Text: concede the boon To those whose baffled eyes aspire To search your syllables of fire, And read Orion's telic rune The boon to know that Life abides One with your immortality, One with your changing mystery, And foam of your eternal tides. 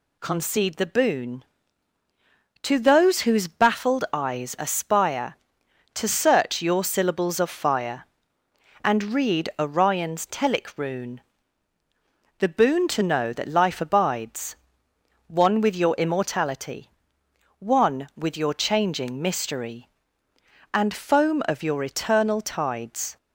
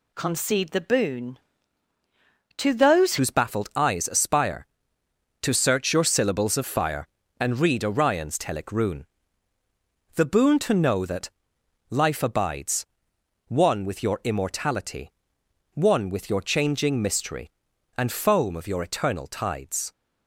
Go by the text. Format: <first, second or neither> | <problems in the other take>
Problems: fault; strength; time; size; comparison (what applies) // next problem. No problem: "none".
first | changes voice at "whose"; from 3.1 s on; 16.8 s long // pauses between "rune" and "The"; at 9.0 s; 1.1 s long; also in the first // pauses between "that" and "Life"; noticeable; at 11.2 s; 0.60 s long // pauses between "abides" and "One"; noticeable; at 12.8 s; 0.62 s long; noticeable in the first